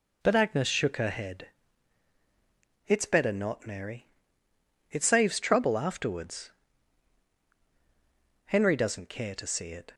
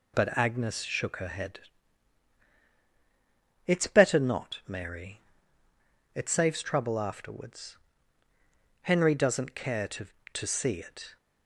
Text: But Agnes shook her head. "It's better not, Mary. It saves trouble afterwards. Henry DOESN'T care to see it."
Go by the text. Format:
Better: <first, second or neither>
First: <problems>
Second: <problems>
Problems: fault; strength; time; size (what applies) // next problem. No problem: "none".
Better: first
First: none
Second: says "to" twice; at 10.3 s